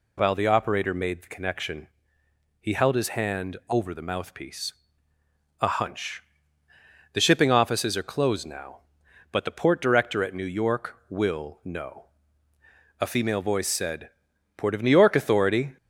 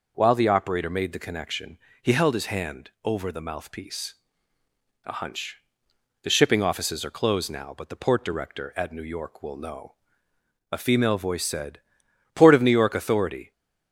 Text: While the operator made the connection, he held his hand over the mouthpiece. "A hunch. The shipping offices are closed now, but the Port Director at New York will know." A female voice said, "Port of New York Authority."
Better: neither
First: none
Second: none

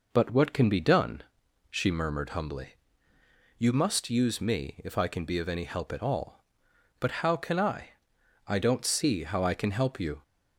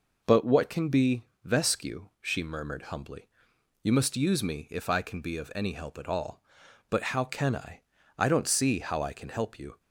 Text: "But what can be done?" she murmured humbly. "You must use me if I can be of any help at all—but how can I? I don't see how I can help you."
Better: first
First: none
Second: says "vescu" for "done"; at 1.4 s

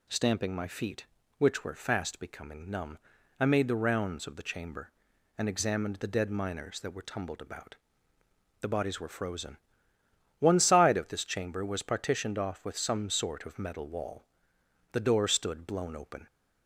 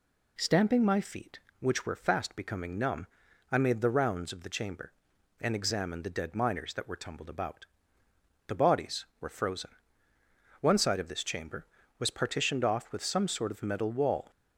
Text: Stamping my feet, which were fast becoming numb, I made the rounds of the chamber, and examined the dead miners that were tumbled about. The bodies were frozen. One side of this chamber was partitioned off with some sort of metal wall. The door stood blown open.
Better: first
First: none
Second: stops before "The door stood blown open"; at 14.3 s

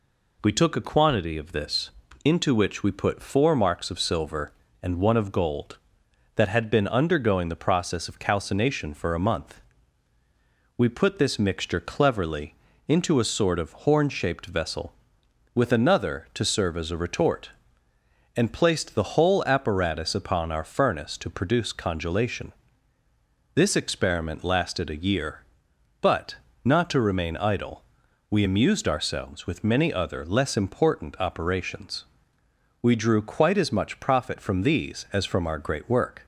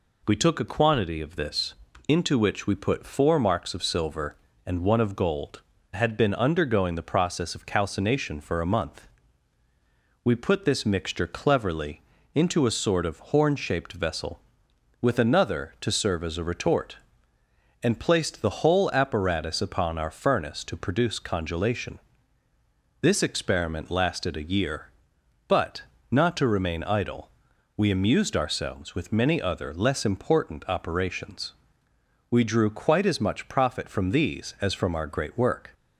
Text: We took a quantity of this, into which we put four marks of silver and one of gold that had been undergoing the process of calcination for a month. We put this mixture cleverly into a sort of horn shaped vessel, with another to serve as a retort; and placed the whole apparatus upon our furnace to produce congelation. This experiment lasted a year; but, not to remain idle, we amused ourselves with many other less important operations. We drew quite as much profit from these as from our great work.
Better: first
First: pauses between "cleverly" and "into"; slight; at 12.5 s; 0.34 s long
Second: skips "that"; at 5.7 s // pauses between "cleverly" and "into"; slight; at 12.0 s; 0.34 s long

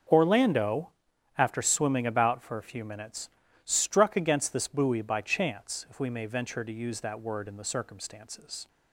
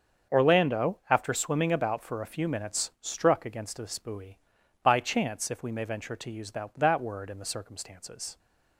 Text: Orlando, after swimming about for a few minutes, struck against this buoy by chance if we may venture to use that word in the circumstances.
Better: first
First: starts louder than the rest; until 1.5 s; 6.5 dB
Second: starts louder than the rest; until 1.4 s; 7 dB // says "that" twice; at 6.7 s

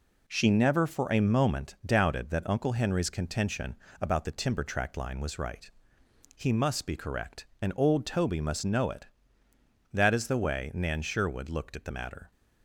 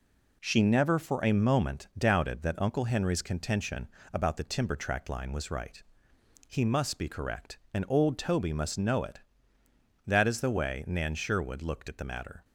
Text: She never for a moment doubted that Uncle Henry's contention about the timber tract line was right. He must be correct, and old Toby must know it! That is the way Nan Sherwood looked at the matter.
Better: neither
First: pauses between "contention" and "about"; slight; at 3.7 s; 0.24 s long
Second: pauses between "contention" and "about"; slight; at 3.8 s; 0.24 s long

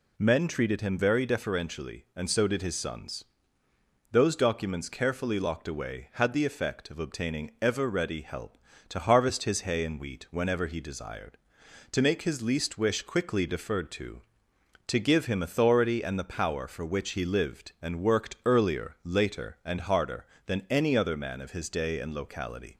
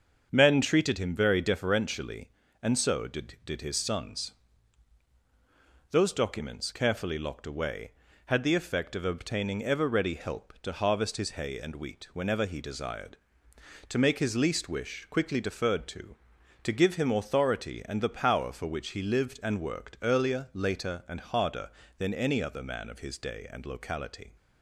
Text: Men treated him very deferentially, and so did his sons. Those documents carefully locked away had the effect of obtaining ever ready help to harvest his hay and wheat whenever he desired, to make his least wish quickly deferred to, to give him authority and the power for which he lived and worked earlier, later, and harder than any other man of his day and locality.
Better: first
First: none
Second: starts louder than the rest; until 1.3 s; 7 dB // says "did" twice; at 3.4 s

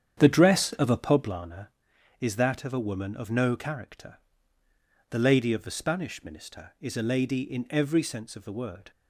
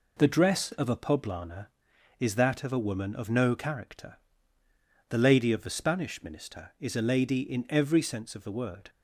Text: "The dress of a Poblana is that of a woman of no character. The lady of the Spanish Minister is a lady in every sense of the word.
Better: second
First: starts louder than the rest; strong; until 1.4 s; 9 dB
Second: none

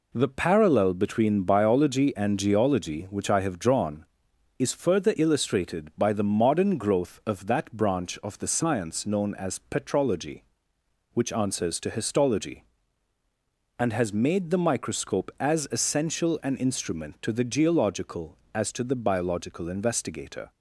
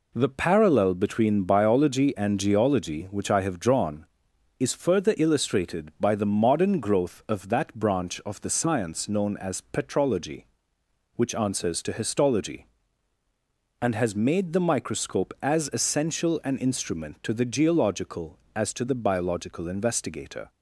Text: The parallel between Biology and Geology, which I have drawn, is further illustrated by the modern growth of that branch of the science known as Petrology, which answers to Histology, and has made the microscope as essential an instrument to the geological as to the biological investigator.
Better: neither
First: none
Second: none

